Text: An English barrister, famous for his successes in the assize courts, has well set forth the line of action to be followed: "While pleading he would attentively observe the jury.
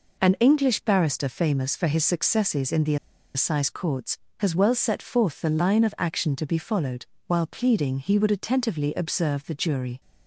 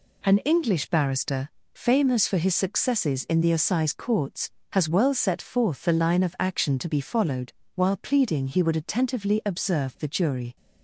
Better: second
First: pauses between "the" and "assize"; at 2.9 s; 0.39 s long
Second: none

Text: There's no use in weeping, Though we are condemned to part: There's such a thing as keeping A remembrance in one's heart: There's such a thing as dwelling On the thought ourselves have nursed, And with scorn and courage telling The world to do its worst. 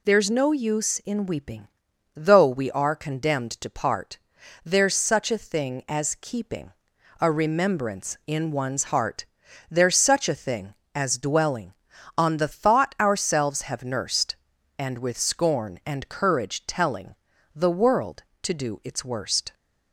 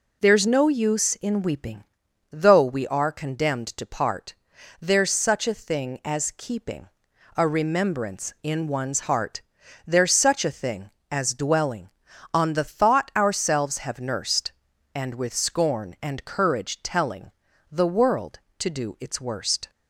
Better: first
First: pauses between "keeping" and "A"; noticeable; at 6.7 s; 0.48 s long // pauses between "telling" and "The"; at 17.1 s; 0.40 s long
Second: starts louder than the rest; slight; until 2.0 s; 3.5 dB // pauses between "keeping" and "A"; noticeable; at 6.8 s; 0.48 s long // pauses between "telling" and "The"; at 17.3 s; 0.40 s long

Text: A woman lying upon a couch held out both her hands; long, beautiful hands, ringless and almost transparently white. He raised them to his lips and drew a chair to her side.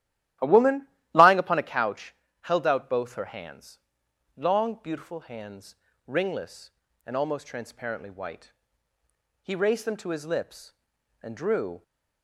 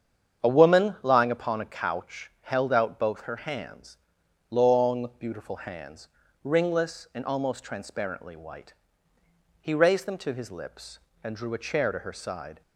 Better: second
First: starts louder than the rest; strong; until 1.6 s; 13 dB // pauses between "woman" and "lying"; slight; at 0.8 s; 0.26 s long // pauses between "couch" and "held"; slight; at 2.1 s; 0.28 s long // stops before "a chair to her side"; at 11.8 s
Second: starts louder than the rest; strong; until 1.4 s; 8 dB

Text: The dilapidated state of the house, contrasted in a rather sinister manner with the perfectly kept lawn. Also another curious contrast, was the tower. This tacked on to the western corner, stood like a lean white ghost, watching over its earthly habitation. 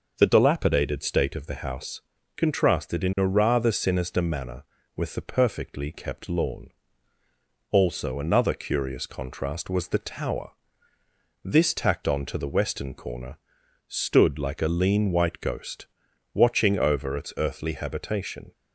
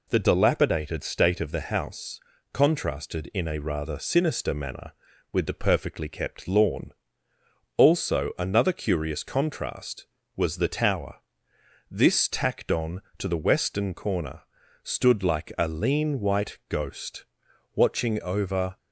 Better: first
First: none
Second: stops before "its earthly habitation"; at 18.7 s

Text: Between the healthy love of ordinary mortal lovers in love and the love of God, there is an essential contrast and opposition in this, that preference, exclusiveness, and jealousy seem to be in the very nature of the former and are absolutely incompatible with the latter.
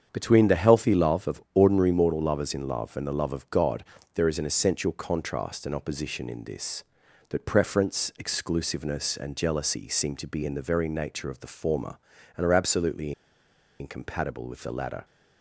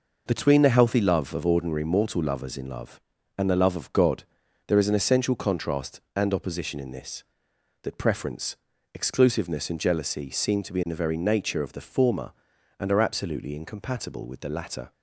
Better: second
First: starts louder than the rest; strong; until 1.1 s; 7.5 dB // pauses between "absolutely" and "incompatible"; noticeable; at 13.1 s; 0.67 s long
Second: none

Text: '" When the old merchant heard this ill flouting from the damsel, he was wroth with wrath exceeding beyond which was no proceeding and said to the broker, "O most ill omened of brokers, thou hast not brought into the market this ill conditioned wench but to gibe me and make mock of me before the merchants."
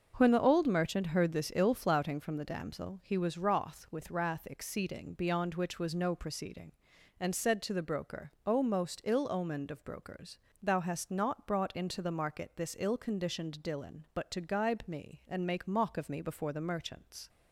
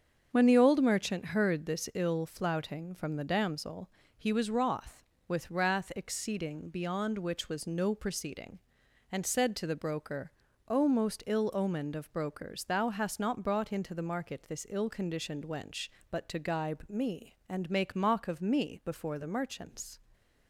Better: second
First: starts louder than the rest; until 1.1 s; 6 dB // says "dillon" for "wench"; at 13.6 s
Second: starts louder than the rest; until 1.3 s; 7 dB

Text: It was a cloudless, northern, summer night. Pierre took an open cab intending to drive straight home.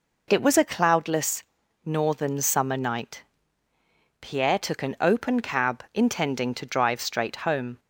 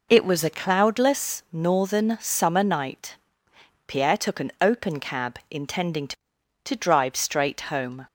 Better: first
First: none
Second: says "to" twice; at 6.6 s

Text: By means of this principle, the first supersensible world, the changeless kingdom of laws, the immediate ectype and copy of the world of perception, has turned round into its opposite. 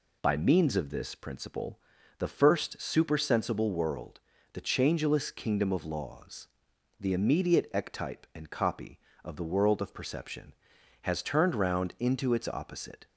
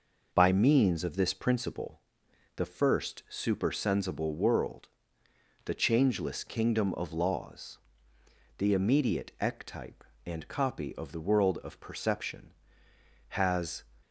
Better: first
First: none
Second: stops before "turned round into its opposite"; at 14.0 s

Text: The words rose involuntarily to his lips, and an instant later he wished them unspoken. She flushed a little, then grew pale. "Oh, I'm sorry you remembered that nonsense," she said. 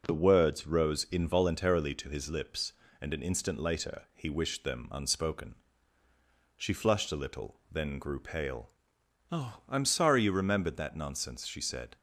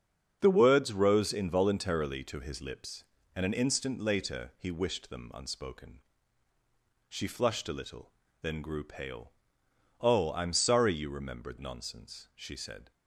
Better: first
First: none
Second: starts louder than the rest; until 1.4 s; 7 dB // skips "that"; at 11.5 s

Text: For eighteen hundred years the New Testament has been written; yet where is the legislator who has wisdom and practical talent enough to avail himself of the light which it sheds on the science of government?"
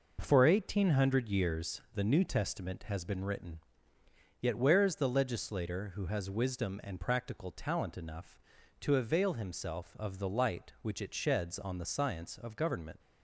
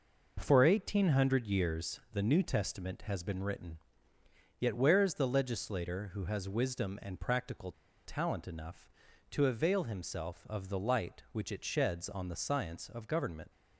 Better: first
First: none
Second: pauses between "practical" and "talent"; slight; at 7.7 s; 0.32 s long

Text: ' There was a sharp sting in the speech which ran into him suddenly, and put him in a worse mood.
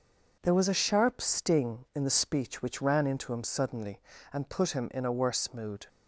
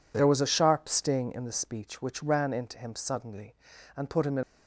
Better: first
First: none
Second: stops before "a worse mood"; at 4.4 s

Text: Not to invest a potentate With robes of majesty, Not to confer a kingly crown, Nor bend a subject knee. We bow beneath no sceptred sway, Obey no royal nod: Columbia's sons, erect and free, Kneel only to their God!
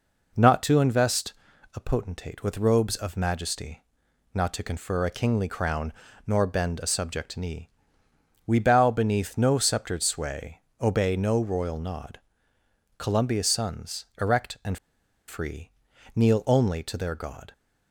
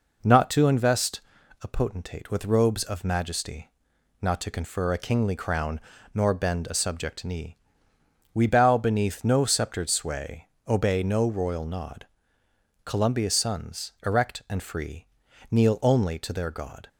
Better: second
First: pauses between "invest" and "a"; at 1.3 s; 0.42 s long // pauses between "and" and "free"; noticeable; at 14.7 s; 0.50 s long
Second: pauses between "invest" and "a"; at 1.2 s; 0.42 s long

